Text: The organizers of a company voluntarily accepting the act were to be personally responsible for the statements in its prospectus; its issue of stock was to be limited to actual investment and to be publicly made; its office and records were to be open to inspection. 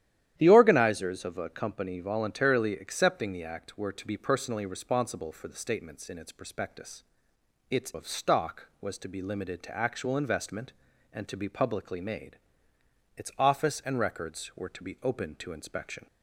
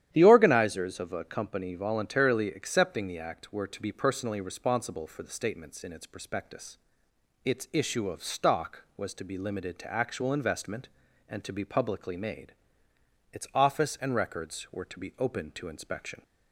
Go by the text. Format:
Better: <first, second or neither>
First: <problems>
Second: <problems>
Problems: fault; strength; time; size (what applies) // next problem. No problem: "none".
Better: second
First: starts louder than the rest; strong; until 1.3 s; 11.5 dB // skips "issue"; at 7.9 s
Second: starts louder than the rest; strong; until 1.1 s; 11 dB